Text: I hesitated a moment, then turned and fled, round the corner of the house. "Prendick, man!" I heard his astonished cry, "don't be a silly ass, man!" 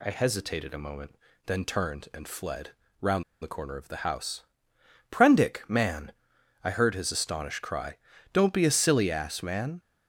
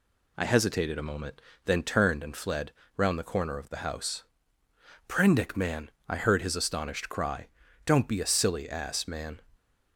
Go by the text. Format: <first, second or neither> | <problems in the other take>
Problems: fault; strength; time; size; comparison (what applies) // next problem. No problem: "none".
second | pauses between "round" and "the"; slight; at 3.2 s; 0.18 s long